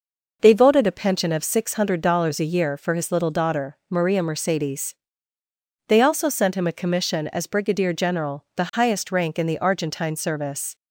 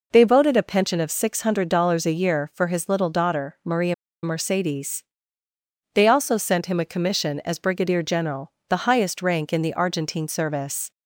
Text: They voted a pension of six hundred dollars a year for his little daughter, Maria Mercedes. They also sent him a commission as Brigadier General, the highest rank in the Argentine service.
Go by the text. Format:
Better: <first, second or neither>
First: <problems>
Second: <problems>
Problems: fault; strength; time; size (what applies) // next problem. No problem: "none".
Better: first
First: none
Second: pauses between "Maria" and "Mercedes"; slight; at 3.9 s; 0.28 s long